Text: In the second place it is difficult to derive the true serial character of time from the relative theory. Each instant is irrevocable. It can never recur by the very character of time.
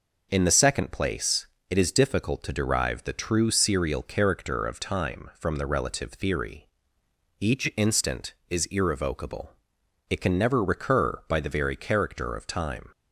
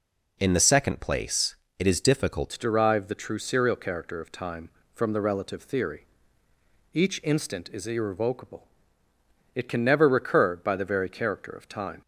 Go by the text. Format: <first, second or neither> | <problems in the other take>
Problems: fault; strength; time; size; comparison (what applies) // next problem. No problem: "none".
first | pauses between "place" and "it"; slight; at 1.5 s; 0.24 s long; slight in the first // changes voice at "to"; from 2.4 s on; 9.6 s long